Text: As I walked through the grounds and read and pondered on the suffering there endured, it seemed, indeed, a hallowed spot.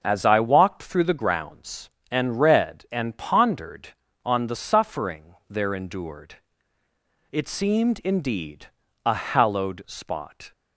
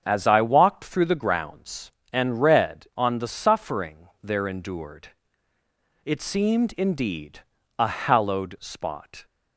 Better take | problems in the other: first | starts louder than the rest; strong; until 1.0 s; 7 dB // skips "and pondered"; at 2.9 s // pauses between "suffering" and "there"; slight; at 4.0 s; 0.16 s long; slight in the first

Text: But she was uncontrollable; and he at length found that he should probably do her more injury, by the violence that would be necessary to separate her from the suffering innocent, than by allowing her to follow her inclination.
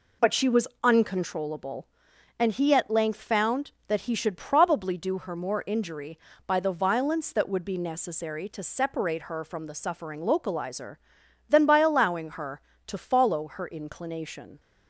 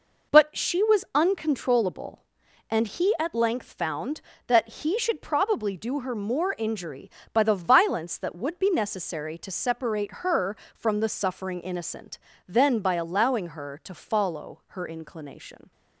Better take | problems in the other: second | pauses between "was" and "uncontrollable"; slight; at 0.6 s; 0.16 s long // says "localizer" for "innocent"; at 10.1 s

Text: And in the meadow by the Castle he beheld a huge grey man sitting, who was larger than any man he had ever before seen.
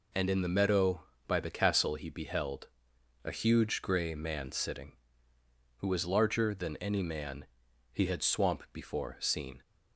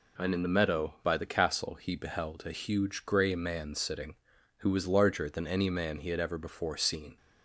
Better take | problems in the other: second | pauses between "beheld" and "a"; noticeable; at 2.6 s; 0.56 s long // pauses between "man" and "he"; noticeable; at 7.4 s; 0.48 s long // says "swamp" for "ever"; at 8.2 s

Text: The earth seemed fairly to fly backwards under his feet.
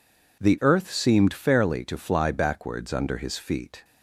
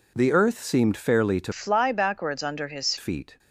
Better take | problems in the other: first | changes voice from "fly" to "his"; from 1.5 to 2.9 s; 1.4 s long

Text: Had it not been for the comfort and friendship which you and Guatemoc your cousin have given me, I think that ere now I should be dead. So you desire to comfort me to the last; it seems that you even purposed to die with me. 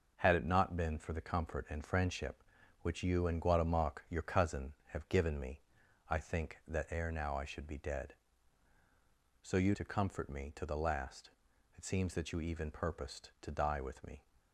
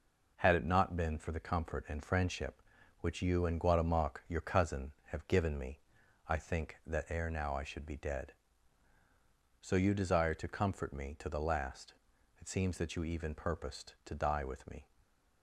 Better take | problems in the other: second | starts louder than the rest; until 1.2 s; 6 dB // skips "desire"; at 9.7 s

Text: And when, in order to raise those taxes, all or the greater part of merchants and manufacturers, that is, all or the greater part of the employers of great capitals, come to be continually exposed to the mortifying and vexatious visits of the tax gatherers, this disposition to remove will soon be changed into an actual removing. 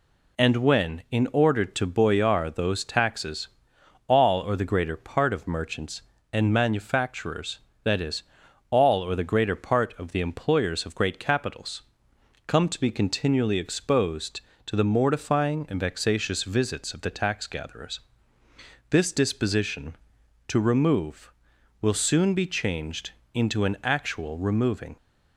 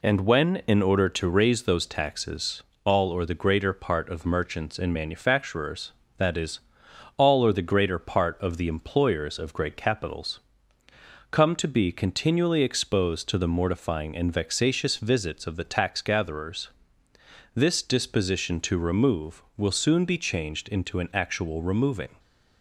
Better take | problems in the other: second | says "boyar" for "raise"; at 1.8 s // pauses between "changed" and "into"; slight; at 23.1 s; 0.24 s long

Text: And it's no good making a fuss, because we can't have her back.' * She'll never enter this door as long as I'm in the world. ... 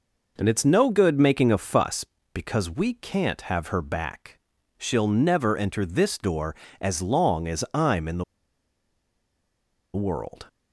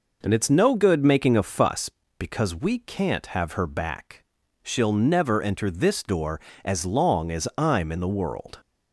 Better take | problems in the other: second | pauses between "the" and "world"; strong; at 8.2 s; 1.7 s long

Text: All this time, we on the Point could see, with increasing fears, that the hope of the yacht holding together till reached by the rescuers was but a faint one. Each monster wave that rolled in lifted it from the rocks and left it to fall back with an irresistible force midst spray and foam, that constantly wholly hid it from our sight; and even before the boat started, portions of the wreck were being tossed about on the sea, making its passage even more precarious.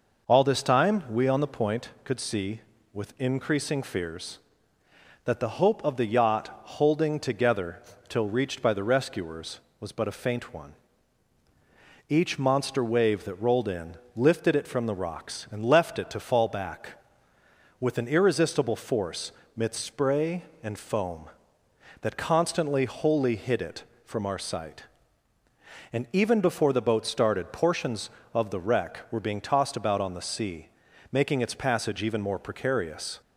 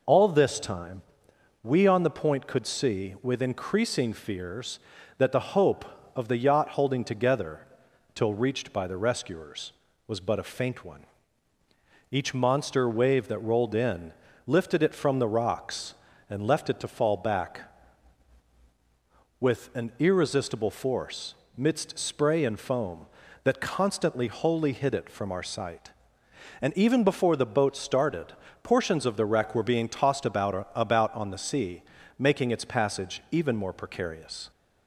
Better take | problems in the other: first | pauses between "together" and "till"; noticeable; at 7.6 s; 0.54 s long; slight in the first // pauses between "in" and "lifted"; slight; at 14.1 s; 0.34 s long; slight in the first // pauses between "force" and "midst"; slight; at 21.3 s; 0.24 s long; slight in the first // says "about" twice; at 30.7 s

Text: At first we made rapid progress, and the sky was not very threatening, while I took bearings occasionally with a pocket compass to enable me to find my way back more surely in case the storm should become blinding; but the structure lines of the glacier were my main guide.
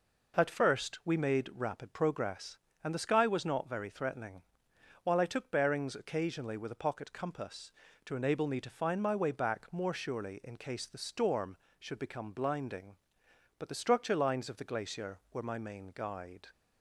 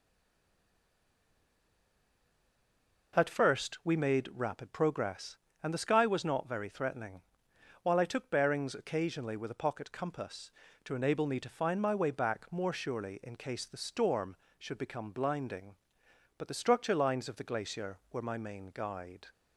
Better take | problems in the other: first | stays silent before the first word; strong; until 3.1 s; 3.1 s long

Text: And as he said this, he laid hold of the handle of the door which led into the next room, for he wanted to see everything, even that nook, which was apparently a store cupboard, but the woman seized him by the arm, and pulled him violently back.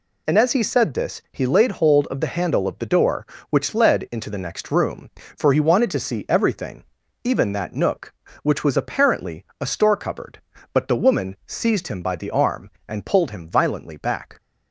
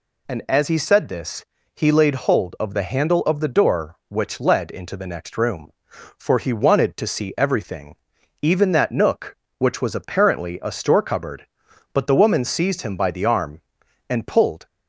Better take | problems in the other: first | stops before "him violently back"; at 14.6 s

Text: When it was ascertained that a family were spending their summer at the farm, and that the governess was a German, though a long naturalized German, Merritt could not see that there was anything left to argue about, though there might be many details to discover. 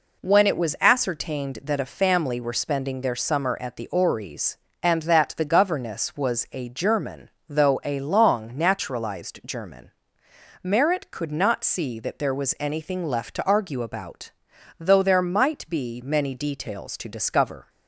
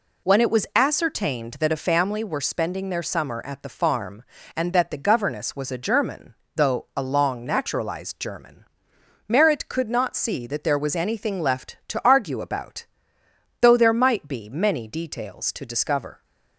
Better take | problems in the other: second | says "ories" for "farm"; at 3.8 s

